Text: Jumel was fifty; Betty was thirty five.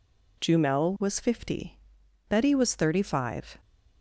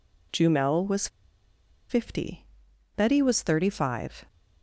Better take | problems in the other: first | pauses between "was" and "fifty"; noticeable; at 1.0 s; 0.82 s long

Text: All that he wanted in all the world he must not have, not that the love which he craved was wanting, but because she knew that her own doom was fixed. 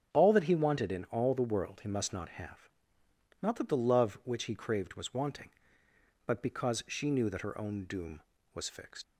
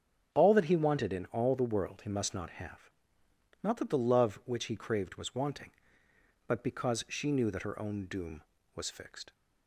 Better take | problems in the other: second | starts louder than the rest; strong; until 1.1 s; 7 dB; strong in the second // leaves "fixed" unfinished; at 9.0 s; 65 ms

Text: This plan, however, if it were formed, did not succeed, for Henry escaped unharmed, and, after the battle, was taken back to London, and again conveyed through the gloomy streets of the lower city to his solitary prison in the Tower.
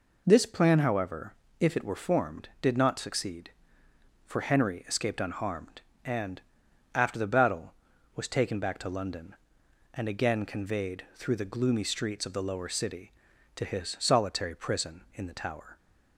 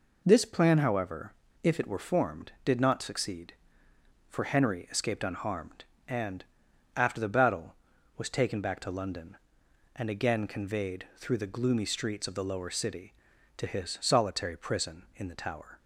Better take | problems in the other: neither | none

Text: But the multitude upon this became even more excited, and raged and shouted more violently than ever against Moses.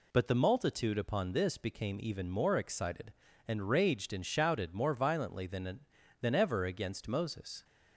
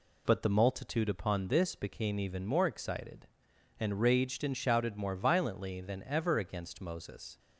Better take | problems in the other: second | says "than" twice; at 6.2 s

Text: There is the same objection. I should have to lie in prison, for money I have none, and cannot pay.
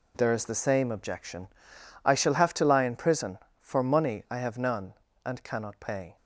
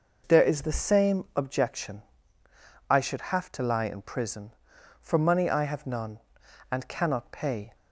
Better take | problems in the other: second | says "shall" for "should"; at 2.1 s

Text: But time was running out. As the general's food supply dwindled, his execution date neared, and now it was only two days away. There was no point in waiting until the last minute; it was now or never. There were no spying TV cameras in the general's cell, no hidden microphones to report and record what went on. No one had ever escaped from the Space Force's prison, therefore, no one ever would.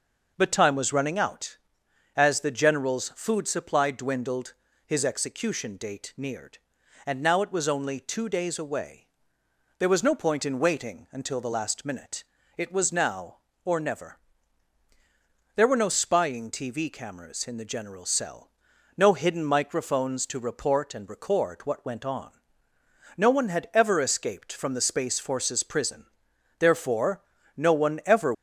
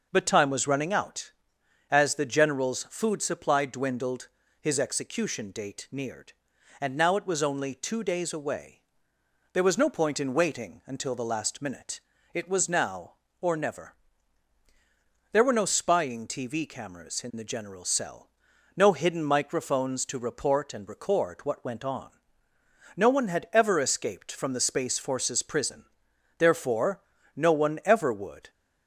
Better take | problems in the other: second | stops before "would"; at 28.3 s

